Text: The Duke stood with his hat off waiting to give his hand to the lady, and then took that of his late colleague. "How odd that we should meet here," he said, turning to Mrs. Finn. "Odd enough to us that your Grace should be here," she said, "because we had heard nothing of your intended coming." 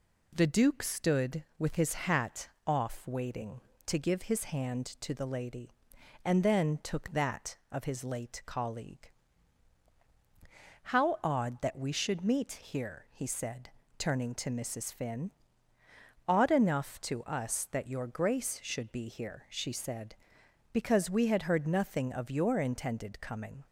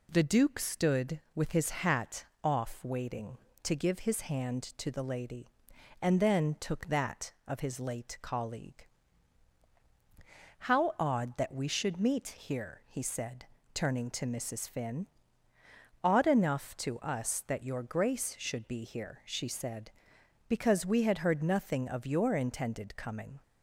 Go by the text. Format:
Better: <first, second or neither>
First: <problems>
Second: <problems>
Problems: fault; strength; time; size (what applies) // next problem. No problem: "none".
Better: neither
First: pauses between "hat" and "off"; slight; at 2.4 s; 0.18 s long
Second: pauses between "hat" and "off"; slight; at 2.2 s; 0.18 s long